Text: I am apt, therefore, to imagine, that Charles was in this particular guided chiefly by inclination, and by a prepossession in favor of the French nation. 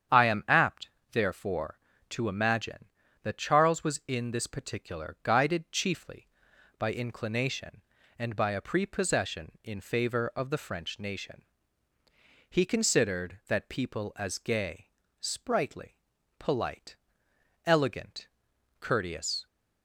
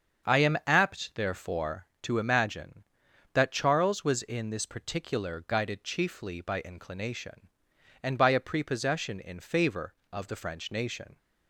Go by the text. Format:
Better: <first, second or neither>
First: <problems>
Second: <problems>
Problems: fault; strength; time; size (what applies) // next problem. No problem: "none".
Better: second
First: starts louder than the rest; strong; until 1.3 s; 8.5 dB // goes on to say "He considered that people as gay sprightly polite elegant courteous"; strong; from 12.4 s on; 6.9 s long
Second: starts louder than the rest; strong; until 1.3 s; 7.5 dB